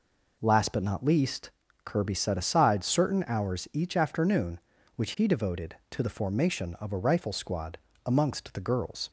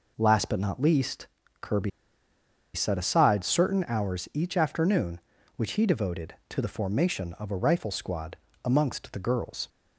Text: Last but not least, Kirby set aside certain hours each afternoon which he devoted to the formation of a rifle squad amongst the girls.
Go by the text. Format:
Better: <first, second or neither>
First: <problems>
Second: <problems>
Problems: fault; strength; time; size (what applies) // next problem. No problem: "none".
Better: first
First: pauses between "squad" and "amongst"; slight; at 7.7 s; 0.28 s long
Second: pauses between "Kirby" and "set"; noticeable; at 1.9 s; 0.84 s long // pauses between "squad" and "amongst"; slight; at 8.3 s; 0.28 s long